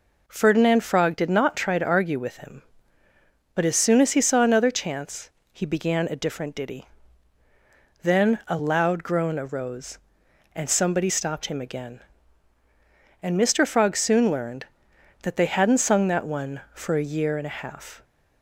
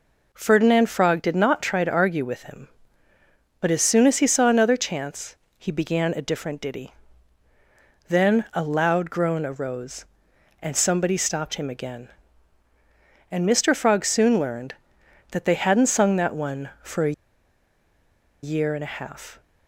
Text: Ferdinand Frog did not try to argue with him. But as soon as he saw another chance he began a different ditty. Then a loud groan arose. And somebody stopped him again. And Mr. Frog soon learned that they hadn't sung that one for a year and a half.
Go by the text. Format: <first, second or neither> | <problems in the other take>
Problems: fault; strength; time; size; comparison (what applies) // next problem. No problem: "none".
first | pauses between "chance" and "he"; slight; at 5.3 s; 0.22 s long; slight in the first // pauses between "a" and "year"; strong; at 17.1 s; 1.3 s long